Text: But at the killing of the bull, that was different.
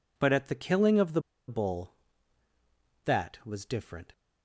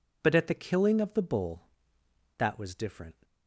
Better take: second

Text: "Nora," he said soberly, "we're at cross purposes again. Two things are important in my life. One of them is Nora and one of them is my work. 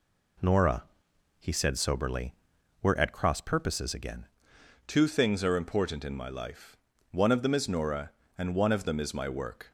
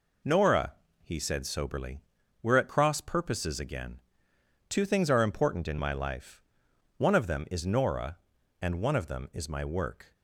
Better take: second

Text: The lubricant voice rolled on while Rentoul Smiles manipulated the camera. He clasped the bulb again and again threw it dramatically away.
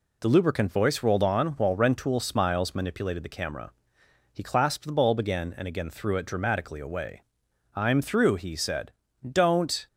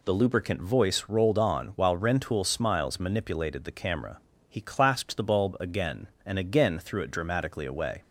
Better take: second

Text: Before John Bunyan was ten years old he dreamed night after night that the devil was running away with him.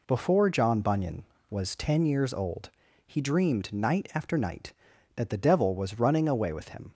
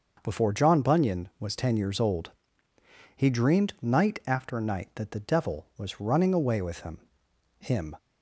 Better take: first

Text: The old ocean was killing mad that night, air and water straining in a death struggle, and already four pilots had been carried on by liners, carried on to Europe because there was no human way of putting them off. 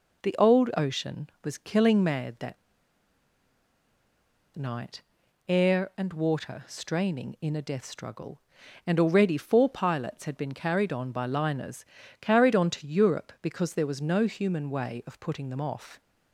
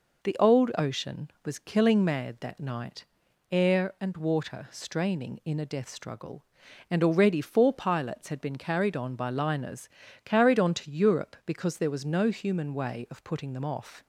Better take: second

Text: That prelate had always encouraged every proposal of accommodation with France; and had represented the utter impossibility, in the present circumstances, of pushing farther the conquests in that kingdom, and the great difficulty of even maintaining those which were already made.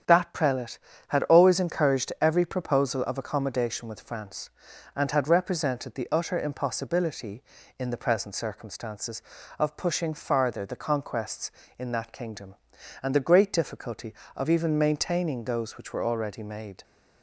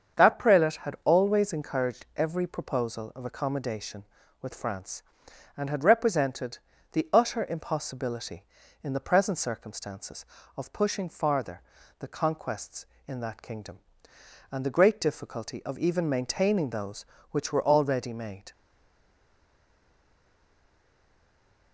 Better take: first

